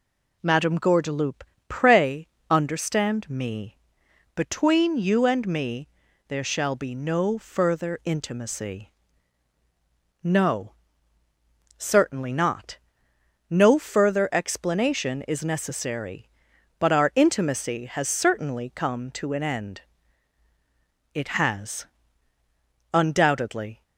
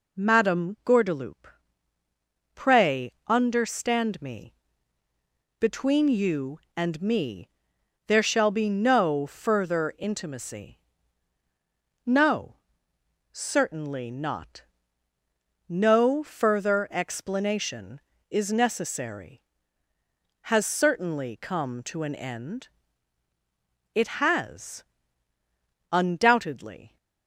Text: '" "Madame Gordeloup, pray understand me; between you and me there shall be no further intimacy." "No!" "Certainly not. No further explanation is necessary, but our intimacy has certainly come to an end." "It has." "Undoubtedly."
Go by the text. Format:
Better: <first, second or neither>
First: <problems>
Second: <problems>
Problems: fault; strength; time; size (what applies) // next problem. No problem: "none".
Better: first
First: pauses between "pray" and "understand"; slight; at 2.2 s; 0.24 s long // pauses between "me" and "there"; at 5.8 s; 0.42 s long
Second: pauses between "pray" and "understand"; slight; at 3.1 s; 0.16 s long // pauses between "me" and "there"; noticeable; at 7.4 s; 0.58 s long // skips "but our intimacy"; at 19.9 s